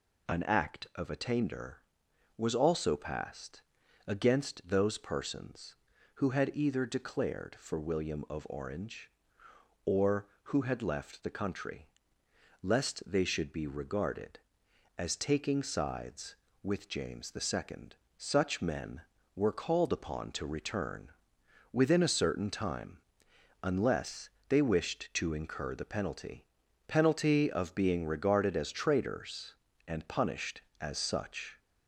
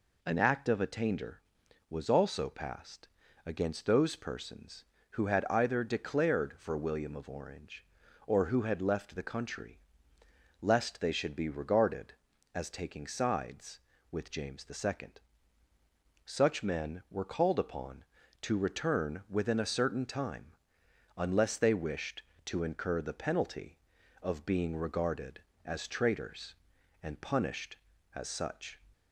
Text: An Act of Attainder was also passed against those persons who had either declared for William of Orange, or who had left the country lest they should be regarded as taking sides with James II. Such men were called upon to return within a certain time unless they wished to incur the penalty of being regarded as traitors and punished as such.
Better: second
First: pauses between "passed" and "against"; noticeable; at 3.6 s; 0.46 s long // pauses between "country" and "lest"; noticeable; at 11.8 s; 0.74 s long // pauses between "return" and "within"; noticeable; at 21.1 s; 0.60 s long // pauses between "time" and "unless"; noticeable; at 22.9 s; 0.64 s long // pauses between "unless" and "they"; slight; at 24.3 s; 0.18 s long // says "penalty" twice; at 26.8 s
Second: pauses between "passed" and "against"; slight; at 3.0 s; 0.36 s long // pauses between "country" and "lest"; noticeable; at 9.7 s; 0.81 s long // pauses between "time" and "unless"; noticeable; at 20.5 s; 0.64 s long

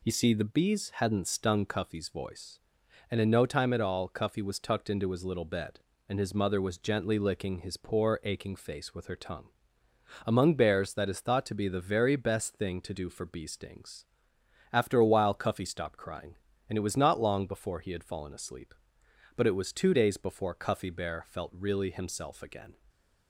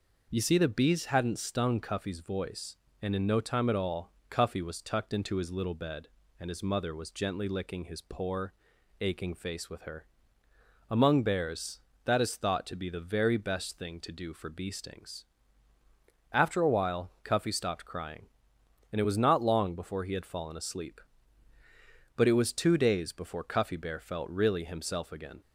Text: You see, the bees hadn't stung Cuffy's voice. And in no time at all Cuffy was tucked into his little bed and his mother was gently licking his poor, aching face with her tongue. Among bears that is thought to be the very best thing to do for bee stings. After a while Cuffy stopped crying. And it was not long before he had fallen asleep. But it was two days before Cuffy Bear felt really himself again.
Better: first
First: none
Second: pauses between "all" and "Cuffy"; slight; at 4.1 s; 0.18 s long // skips "tongue"; at 10.4 s

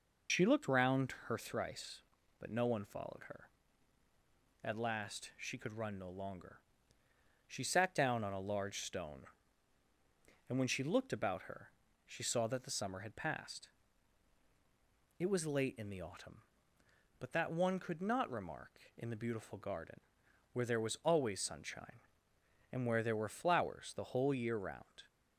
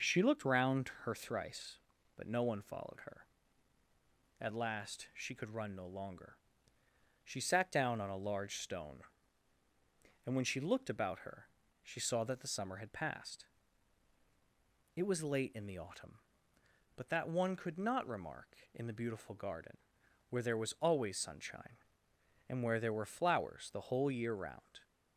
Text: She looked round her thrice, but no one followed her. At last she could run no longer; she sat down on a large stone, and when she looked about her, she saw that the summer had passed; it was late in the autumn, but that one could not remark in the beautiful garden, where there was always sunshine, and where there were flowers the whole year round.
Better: second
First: loses the start of "She"; at 0.2 s; 65 ms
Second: none

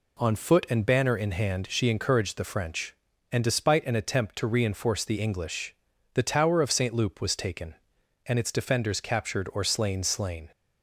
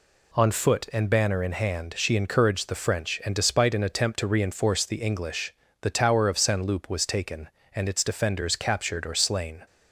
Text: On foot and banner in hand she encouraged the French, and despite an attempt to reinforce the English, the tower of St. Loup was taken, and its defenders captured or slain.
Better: second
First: says "slain" twice; at 10.0 s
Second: none

